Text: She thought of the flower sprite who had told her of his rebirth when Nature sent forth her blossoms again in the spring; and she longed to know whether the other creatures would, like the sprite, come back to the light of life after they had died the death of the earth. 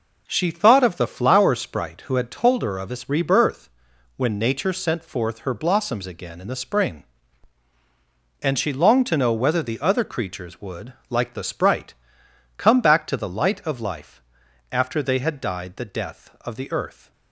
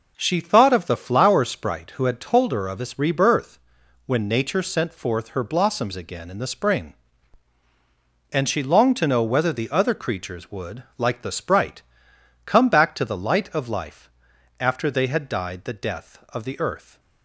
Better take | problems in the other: neither | pauses between "rebirth" and "when"; noticeable; the same in both // pauses between "life" and "after"; noticeable; the same in both

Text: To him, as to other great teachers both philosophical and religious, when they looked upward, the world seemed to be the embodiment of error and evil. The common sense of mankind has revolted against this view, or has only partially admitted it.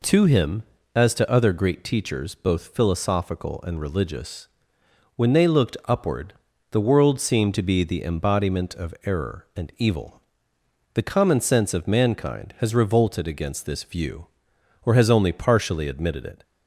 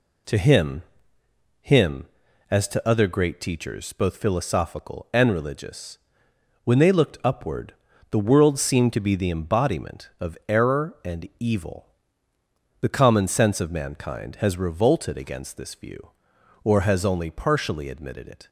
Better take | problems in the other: first | says "him" twice; at 1.6 s

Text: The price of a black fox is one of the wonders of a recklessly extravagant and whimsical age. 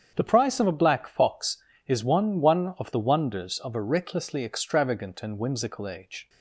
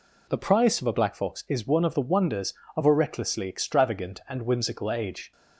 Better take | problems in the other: second | starts louder than the rest; strong; until 1.1 s; 8 dB // says "one" twice; at 2.3 s

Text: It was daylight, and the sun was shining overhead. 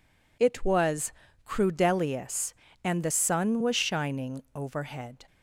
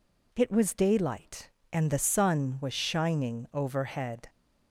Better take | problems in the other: second | says "crudelius" for "daylight"; at 1.4 s

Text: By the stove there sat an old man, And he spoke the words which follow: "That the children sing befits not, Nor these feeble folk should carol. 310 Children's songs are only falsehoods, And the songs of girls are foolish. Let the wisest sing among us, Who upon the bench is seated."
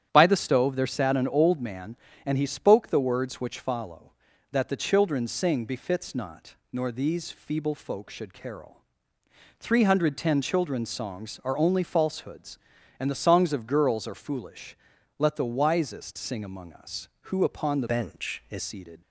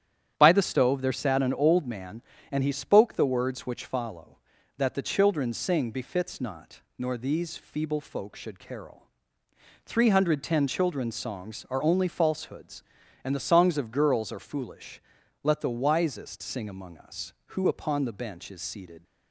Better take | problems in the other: second | starts louder than the rest; strong; until 1.1 s; 10.5 dB; strong in the second // changes voice from "bench" to "is"; from 17.8 to 18.6 s; 0.8 s long

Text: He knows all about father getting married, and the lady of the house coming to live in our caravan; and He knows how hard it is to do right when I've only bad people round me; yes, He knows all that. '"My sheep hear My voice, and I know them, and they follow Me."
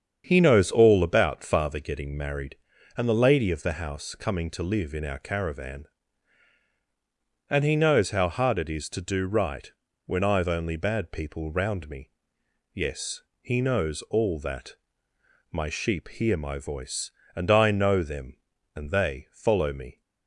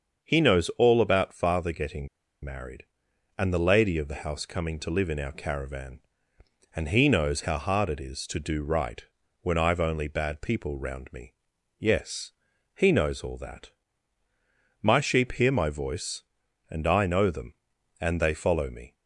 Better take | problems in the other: first | starts louder than the rest; until 1.2 s; 6.5 dB; strong in the first // pauses between "getting" and "married"; slight; at 2.0 s; 0.36 s long // pauses between "right" and "when"; at 9.0 s; 0.38 s long; slight in the first

